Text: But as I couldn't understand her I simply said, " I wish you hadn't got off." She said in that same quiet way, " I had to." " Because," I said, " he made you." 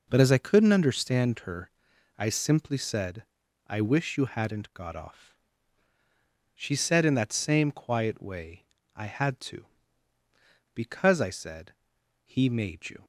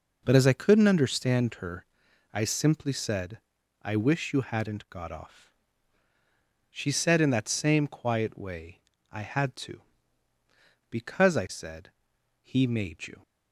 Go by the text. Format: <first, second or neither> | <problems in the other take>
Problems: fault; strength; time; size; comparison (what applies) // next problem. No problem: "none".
neither | starts louder than the rest; the same in both // pauses between "her" and "I"; noticeable; the same in both